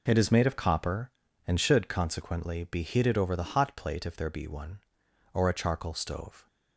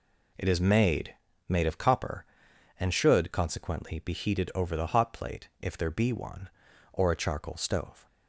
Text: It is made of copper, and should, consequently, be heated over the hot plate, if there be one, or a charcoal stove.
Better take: first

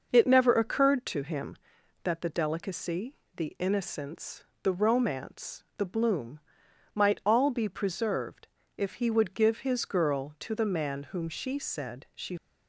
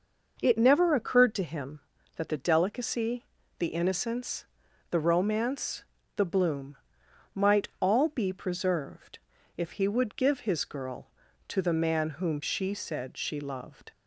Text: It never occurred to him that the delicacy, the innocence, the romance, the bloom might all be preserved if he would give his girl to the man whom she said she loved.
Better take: second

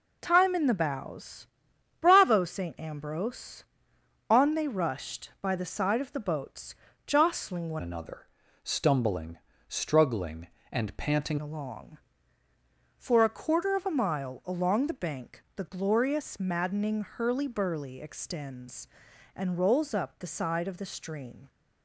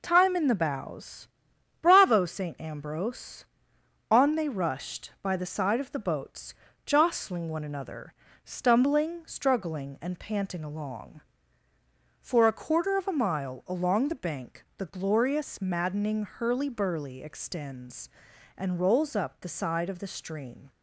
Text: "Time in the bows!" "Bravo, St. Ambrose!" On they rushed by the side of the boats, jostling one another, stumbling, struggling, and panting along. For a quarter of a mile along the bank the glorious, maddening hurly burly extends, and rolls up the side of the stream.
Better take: second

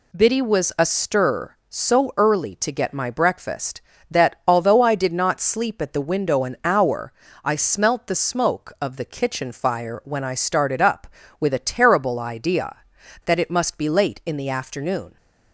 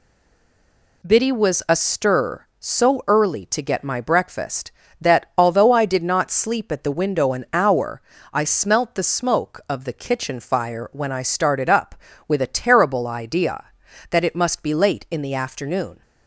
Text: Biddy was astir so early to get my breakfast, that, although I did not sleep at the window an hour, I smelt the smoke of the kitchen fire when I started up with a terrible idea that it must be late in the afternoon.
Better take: first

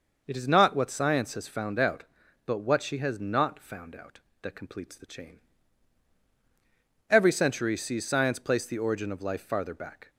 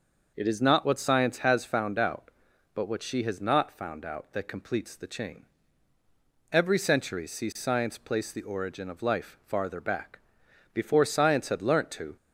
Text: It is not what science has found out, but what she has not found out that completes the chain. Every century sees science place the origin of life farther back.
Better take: first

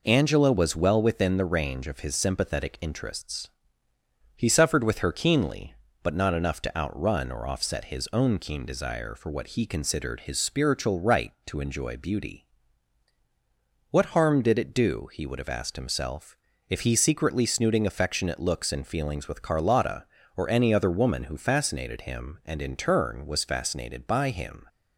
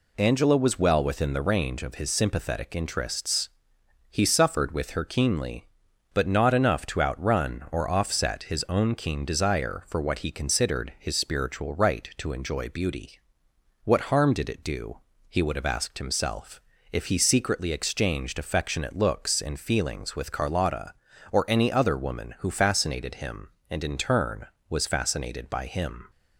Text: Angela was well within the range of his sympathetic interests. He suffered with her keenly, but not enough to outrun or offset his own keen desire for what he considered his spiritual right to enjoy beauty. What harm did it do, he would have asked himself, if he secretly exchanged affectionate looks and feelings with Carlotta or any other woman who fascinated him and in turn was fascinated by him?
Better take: second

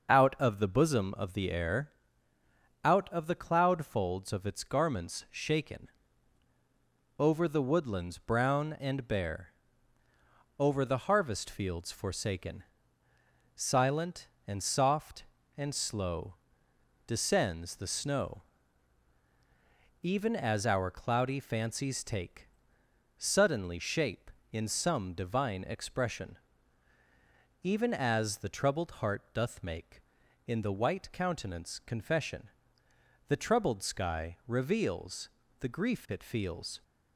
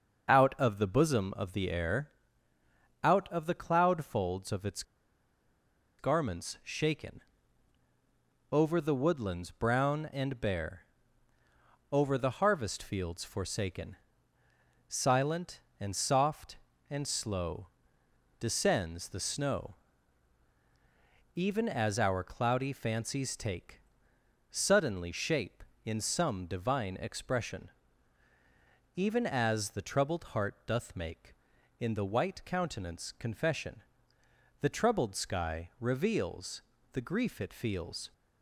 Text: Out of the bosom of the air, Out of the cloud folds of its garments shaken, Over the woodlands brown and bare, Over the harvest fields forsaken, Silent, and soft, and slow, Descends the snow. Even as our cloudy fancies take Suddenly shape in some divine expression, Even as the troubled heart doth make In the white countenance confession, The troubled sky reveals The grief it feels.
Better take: first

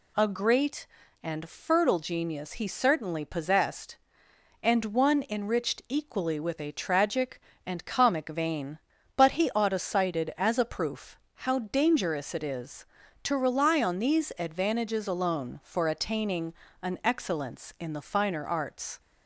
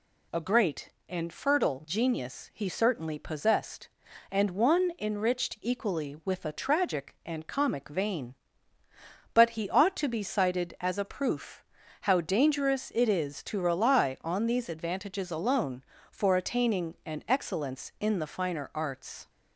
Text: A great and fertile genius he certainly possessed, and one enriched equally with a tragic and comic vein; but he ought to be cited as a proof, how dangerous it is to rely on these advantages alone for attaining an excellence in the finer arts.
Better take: second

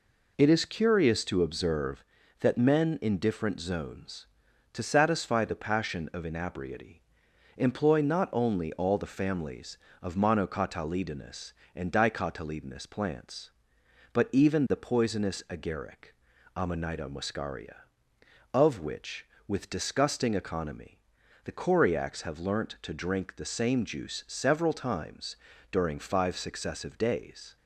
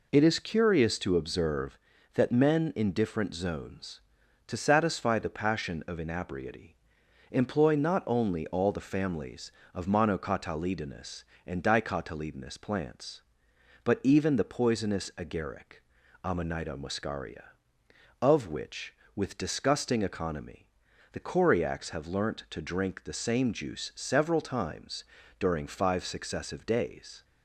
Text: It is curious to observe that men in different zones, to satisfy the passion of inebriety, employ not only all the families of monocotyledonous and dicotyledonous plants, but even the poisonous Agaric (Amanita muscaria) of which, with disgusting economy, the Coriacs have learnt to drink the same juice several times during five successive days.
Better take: neither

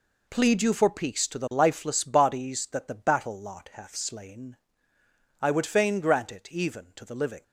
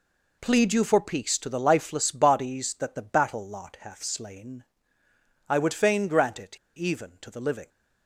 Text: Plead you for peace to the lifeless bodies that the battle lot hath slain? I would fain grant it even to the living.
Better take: first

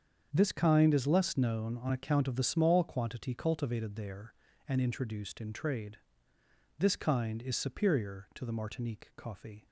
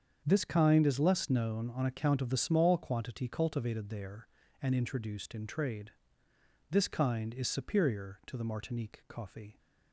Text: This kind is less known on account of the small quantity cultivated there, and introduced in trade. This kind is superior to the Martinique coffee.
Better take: neither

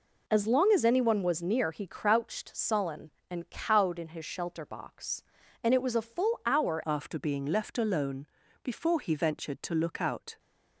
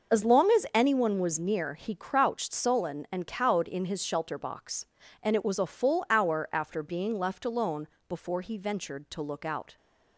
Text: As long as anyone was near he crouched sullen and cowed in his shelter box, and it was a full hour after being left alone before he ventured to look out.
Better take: second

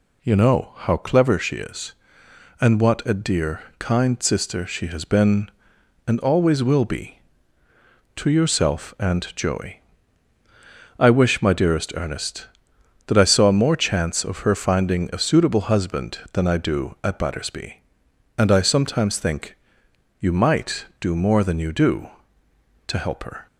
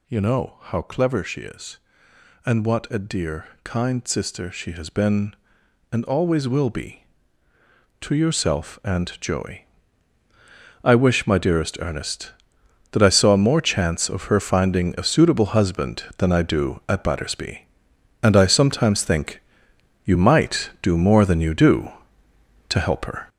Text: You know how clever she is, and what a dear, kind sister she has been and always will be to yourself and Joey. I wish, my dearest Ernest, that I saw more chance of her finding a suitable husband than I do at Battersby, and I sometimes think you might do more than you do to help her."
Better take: first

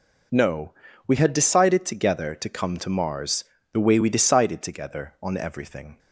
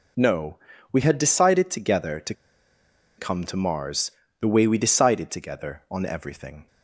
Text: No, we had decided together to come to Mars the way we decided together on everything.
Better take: first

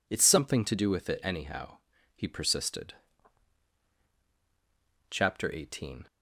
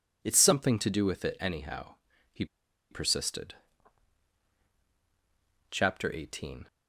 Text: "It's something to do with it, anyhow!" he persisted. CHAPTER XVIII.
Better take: first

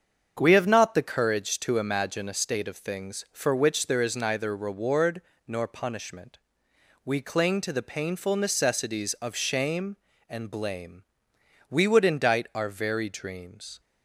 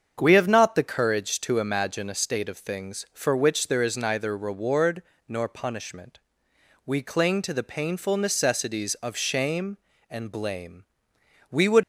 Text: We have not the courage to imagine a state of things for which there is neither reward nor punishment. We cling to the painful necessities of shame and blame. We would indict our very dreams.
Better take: first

